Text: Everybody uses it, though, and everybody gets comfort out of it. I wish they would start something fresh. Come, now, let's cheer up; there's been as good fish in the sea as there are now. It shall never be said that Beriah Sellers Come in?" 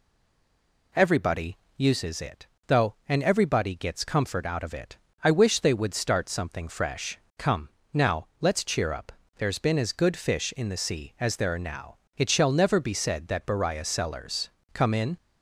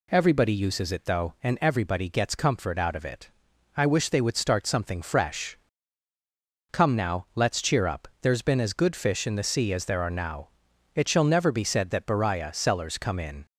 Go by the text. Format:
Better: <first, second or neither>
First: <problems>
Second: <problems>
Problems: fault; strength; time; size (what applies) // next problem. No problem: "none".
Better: second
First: stays silent before the first word; slight; until 0.9 s; 0.9 s long // pauses between "Everybody" and "uses"; slight; at 1.5 s; 0.22 s long // pauses between "Sellers" and "Come"; slight; at 14.5 s; 0.24 s long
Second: none